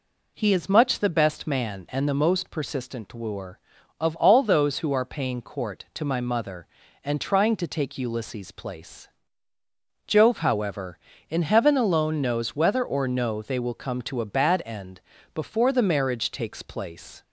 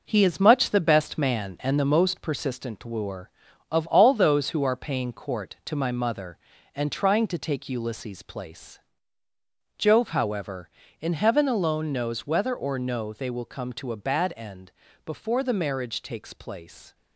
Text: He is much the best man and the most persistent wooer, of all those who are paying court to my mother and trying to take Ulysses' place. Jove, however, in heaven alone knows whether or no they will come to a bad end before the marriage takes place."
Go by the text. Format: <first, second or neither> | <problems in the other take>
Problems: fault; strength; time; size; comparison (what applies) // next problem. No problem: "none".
first | gets quieter; throughout; 6 dB // pauses between "end" and "before"; slight; at 14.7 s; 0.34 s long; slight in the first